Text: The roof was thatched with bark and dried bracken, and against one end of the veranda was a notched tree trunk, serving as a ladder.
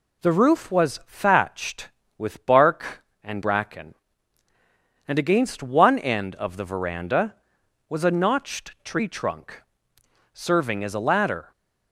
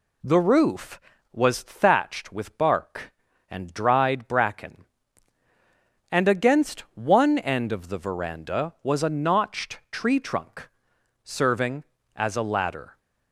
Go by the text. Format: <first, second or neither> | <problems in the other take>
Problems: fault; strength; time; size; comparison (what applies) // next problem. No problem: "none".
second | skips "dried"; at 3.4 s